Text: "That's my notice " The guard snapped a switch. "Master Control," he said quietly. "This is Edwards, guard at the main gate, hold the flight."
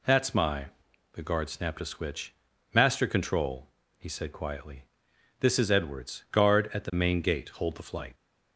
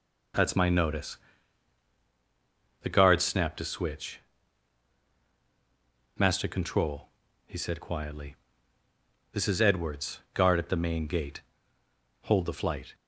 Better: second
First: skips "notice"; at 0.7 s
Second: none

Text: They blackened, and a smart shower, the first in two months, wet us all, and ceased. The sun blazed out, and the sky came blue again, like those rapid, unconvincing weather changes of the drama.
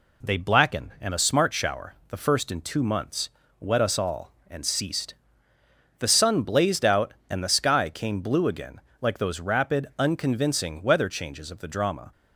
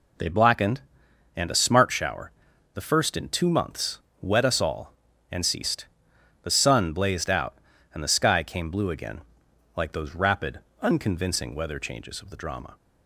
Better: neither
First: none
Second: none

